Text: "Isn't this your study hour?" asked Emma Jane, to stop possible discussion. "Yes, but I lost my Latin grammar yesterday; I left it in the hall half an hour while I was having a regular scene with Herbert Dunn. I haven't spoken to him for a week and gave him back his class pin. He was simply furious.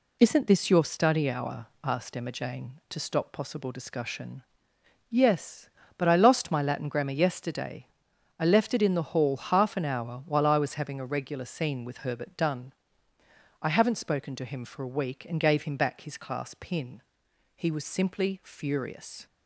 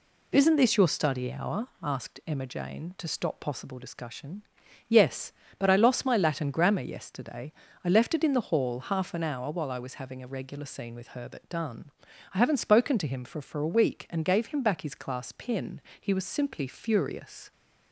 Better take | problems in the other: first | says "for" twice; at 13.4 s

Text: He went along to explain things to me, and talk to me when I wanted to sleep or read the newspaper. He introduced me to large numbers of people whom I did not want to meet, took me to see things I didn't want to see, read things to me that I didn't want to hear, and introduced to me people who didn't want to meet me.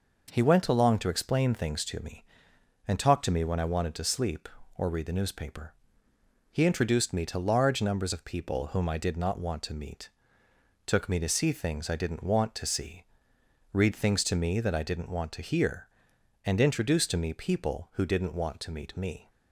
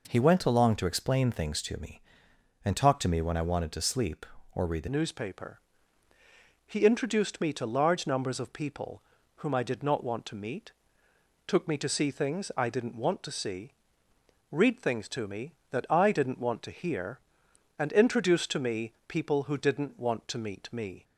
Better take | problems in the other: first | changes voice at "newspaper"; from 4.8 s on; 16.2 s long // pauses between "people" and "whom"; slight; at 9.0 s; 0.34 s long // pauses between "me" and "people"; slight; at 18.9 s; 0.18 s long

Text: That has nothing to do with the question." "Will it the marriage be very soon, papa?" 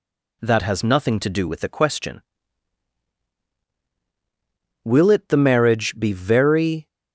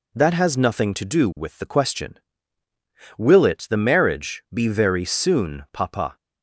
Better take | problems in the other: second | stops before "soon papa"; at 6.8 s

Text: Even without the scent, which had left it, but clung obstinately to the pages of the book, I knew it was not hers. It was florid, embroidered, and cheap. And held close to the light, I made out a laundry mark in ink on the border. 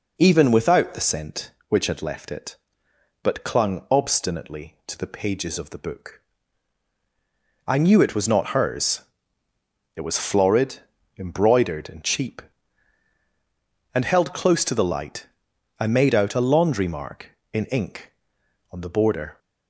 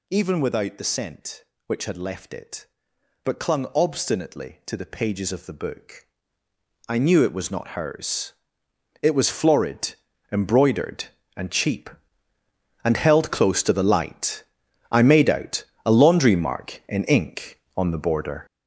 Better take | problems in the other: first | gets louder; strong; throughout; 8.5 dB // pauses between "out" and "a"; slight; at 15.6 s; 0.20 s long

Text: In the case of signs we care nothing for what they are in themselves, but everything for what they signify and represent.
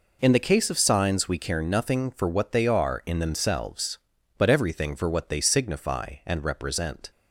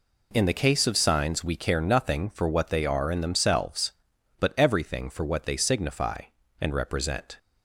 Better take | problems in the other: neither | none

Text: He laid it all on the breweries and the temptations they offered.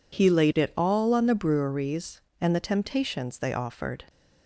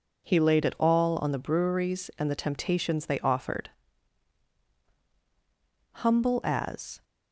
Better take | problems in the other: first | goes on to say "Humble as"; noticeable; from 5.9 s on; 1.0 s long

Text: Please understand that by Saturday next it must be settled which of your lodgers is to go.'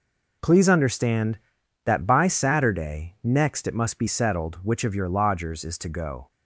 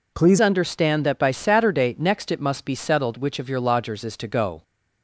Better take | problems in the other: first | changes voice at "understand"; from 0.4 s on; 4.2 s long

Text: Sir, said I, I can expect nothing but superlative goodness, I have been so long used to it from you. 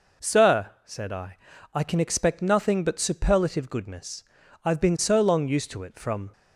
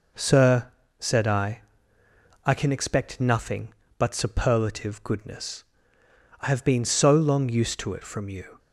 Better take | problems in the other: second | stops before "you"; at 6.3 s

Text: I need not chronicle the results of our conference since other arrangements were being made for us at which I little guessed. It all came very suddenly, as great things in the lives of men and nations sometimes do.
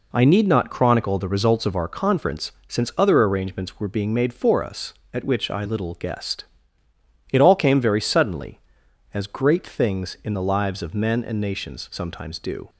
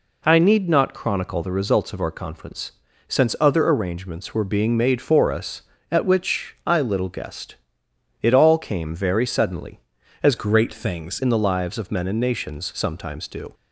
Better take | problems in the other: first | pauses between "conference" and "since"; at 2.7 s; 0.38 s long // changes voice from "great" to "things"; from 10.3 to 11.1 s; 0.8 s long

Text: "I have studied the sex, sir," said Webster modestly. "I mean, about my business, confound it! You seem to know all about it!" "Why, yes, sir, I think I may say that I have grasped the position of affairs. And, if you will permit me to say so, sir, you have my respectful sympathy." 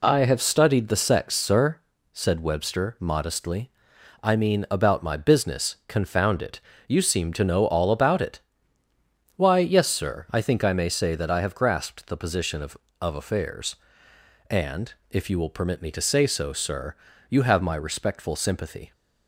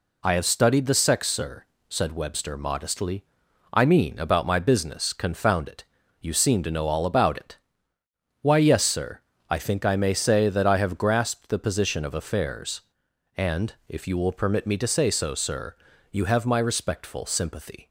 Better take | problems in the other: second | says "of" twice; at 12.9 s

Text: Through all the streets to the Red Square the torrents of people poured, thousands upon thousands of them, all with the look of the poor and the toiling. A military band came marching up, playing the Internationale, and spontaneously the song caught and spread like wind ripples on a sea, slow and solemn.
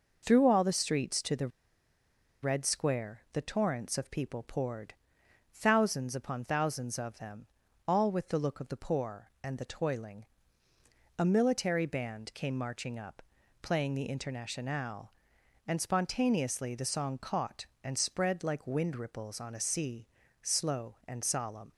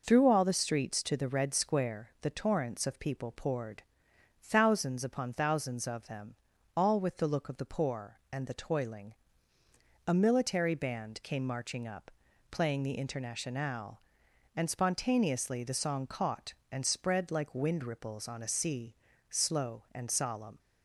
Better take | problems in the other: second | pauses between "the" and "Red"; noticeable; at 1.4 s; 0.94 s long

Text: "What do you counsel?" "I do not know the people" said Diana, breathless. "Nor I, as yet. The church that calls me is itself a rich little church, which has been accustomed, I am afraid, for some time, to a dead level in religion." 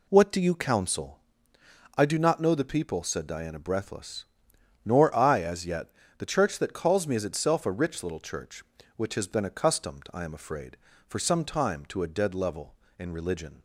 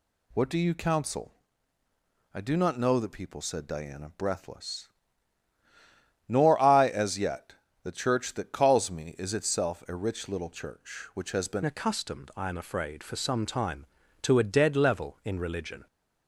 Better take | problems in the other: first | changes voice at "accustomed"; from 11.6 s on; 4.2 s long

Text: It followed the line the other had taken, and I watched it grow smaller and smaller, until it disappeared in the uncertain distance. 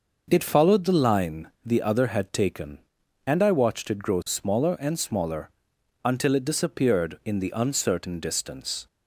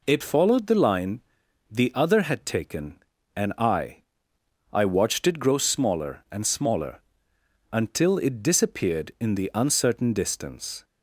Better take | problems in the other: first | pauses between "line" and "the"; noticeable; at 1.2 s; 0.50 s long; slight in the first // says "I" twice; at 4.7 s

